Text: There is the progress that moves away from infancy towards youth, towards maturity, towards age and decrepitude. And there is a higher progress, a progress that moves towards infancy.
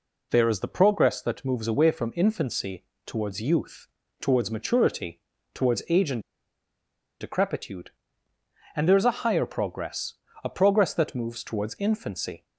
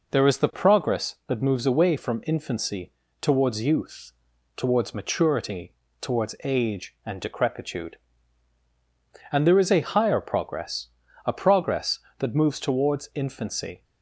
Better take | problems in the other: second | pauses between "infancy" and "towards"; slight; at 2.8 s; 0.22 s long; slight in the second // pauses between "and" and "decrepitude"; at 6.2 s; 0.98 s long

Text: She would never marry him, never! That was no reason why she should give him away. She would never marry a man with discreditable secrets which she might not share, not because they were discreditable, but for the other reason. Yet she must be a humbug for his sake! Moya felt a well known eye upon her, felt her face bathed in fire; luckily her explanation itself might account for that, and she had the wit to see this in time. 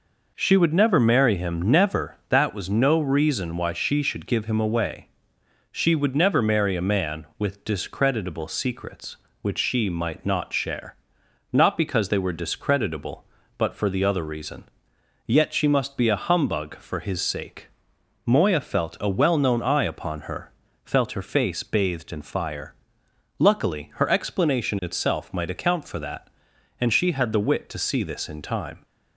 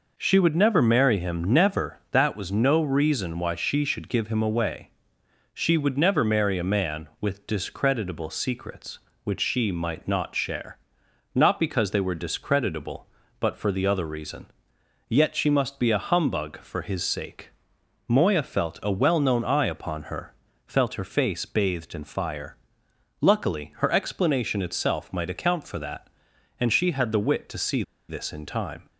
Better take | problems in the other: first | pauses between "see" and "this"; slight; at 27.8 s; 0.27 s long

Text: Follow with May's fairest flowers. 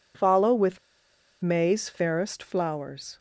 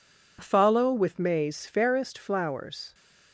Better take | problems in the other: second | pauses between "with" and "May's"; noticeable; at 0.7 s; 0.63 s long

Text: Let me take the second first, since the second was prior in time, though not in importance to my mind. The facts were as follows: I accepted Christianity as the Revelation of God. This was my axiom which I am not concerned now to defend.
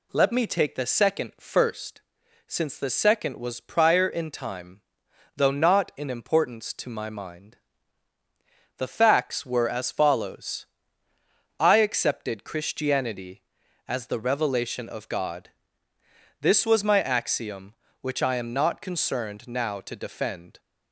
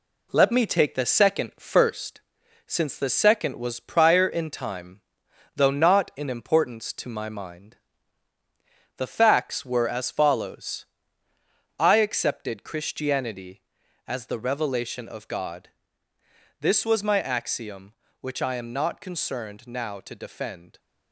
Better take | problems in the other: first | gets quieter; noticeable; throughout; 5.5 dB

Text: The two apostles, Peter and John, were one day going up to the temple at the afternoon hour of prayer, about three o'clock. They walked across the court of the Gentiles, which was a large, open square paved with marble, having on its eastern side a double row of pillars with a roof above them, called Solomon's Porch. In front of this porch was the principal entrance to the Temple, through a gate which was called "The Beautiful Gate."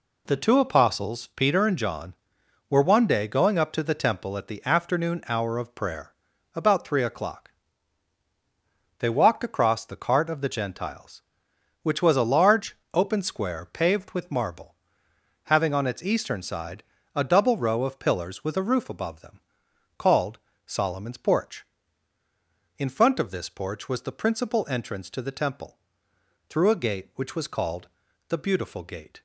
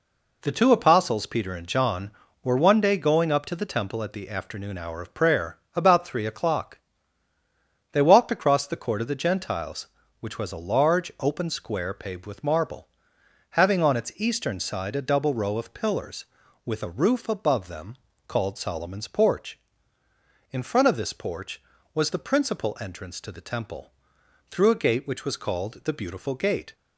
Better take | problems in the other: second | says "cart" for "court"; at 9.9 s // pauses between "side" and "a"; slight; at 16.8 s; 0.32 s long // pauses between "called" and "Solomon's"; slight; at 20.3 s; 0.26 s long // pauses between "called" and "The"; at 27.8 s; 0.44 s long

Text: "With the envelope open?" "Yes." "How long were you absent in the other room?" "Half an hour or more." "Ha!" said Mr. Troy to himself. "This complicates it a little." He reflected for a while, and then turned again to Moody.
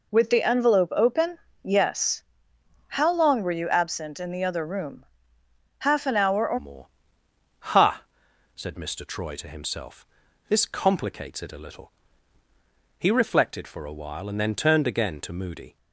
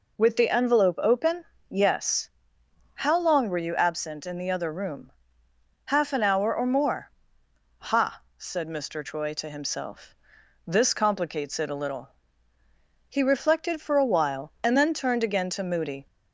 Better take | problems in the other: second | changes voice at "more"; from 6.5 s on; 9.2 s long

